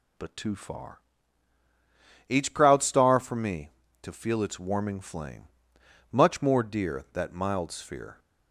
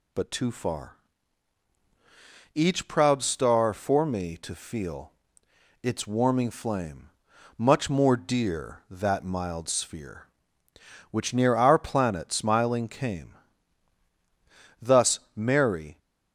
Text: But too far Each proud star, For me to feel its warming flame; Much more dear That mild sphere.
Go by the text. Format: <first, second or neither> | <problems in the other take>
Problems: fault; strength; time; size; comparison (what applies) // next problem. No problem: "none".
first | pauses between "far" and "Each"; strong; at 0.9 s; 1.5 s long; strong in the first // pauses between "feel" and "its"; noticeable; at 5.1 s; 0.70 s long // goes on to say "Which near our planet smiling came Thus Mary"; strong; from 11.1 s on; 4.8 s long